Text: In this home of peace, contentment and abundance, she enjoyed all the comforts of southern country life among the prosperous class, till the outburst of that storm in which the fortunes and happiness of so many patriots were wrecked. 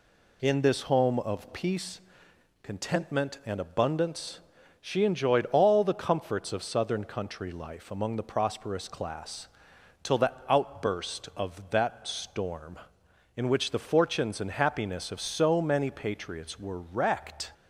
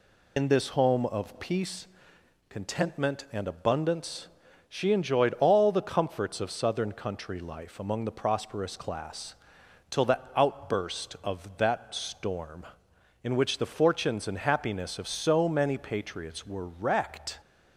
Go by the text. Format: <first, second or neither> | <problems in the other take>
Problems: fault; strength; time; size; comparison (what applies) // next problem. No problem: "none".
first | loses the start of "In"; at 0.3 s; 80 ms // pauses between "the" and "outburst"; slight; at 10.1 s; 0.16 s long; slight in the first